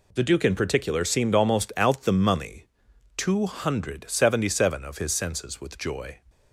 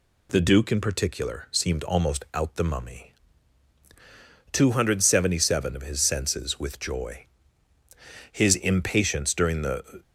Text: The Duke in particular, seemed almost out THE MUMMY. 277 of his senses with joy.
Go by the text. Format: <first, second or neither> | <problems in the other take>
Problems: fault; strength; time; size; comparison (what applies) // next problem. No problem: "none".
first | goes on to say "His impatience during the"; strong; from 8.3 s on; 1.7 s long